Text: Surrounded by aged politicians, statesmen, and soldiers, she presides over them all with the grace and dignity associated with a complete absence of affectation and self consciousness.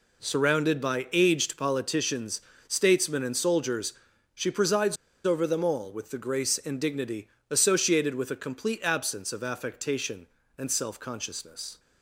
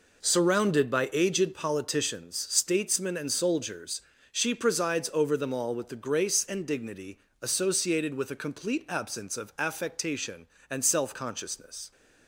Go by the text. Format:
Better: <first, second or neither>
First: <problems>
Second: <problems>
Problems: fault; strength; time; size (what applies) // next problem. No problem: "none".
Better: second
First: pauses between "presides" and "over"; slight; at 4.9 s; 0.29 s long // pauses between "dignity" and "associated"; slight; at 7.2 s; 0.24 s long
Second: pauses between "dignity" and "associated"; slight; at 7.1 s; 0.22 s long